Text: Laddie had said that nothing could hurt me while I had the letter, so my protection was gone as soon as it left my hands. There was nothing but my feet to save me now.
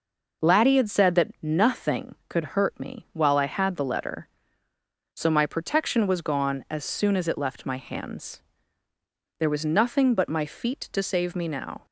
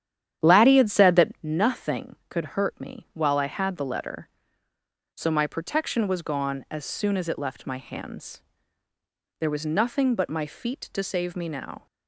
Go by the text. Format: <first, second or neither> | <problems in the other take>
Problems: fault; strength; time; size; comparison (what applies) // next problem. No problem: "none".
first | starts louder than the rest; strong; until 1.5 s; 10.5 dB